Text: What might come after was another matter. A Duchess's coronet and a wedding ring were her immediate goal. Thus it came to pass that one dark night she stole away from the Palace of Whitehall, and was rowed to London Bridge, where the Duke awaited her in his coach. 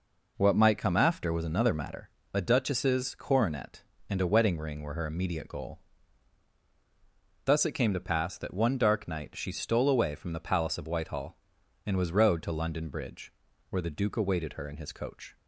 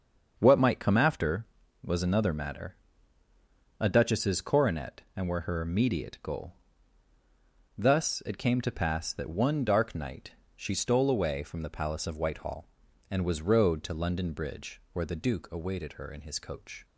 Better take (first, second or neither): first